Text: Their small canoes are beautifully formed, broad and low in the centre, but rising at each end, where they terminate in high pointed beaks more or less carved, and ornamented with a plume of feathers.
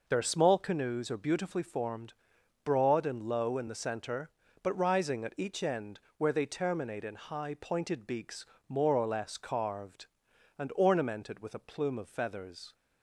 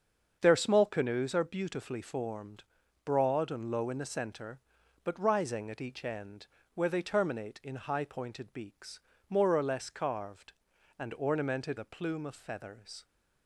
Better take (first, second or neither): first